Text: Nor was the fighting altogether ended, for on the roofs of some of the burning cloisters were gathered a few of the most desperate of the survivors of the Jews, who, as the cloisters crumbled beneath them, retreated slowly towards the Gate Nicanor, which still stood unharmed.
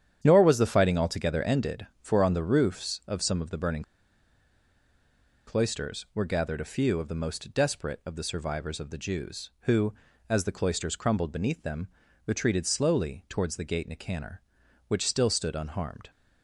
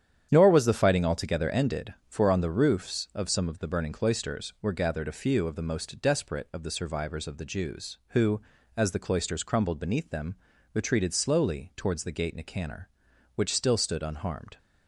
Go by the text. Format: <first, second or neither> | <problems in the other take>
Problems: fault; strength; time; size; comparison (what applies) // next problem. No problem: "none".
second | starts louder than the rest; strong; until 1.2 s; 9.5 dB; strong in the second // pauses between "burning" and "cloisters"; strong; at 3.8 s; 1.6 s long